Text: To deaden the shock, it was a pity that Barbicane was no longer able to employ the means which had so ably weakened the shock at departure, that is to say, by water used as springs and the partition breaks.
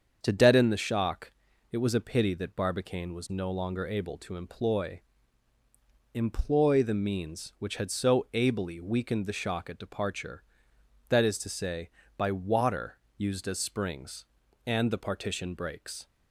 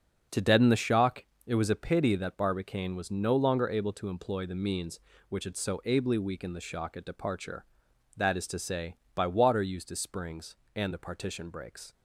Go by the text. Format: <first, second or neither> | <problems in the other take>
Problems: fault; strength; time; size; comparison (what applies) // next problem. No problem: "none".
second | starts louder than the rest; strong; until 1.2 s; 7 dB; also in the second // says "employ" twice; at 6.1 s // pauses between "water" and "used"; slight; at 12.9 s; 0.18 s long